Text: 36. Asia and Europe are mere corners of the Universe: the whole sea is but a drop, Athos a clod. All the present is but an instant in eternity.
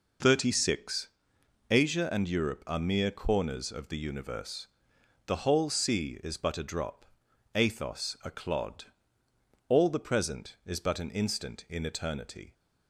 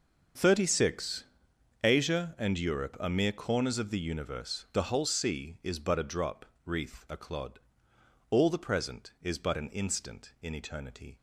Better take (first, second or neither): first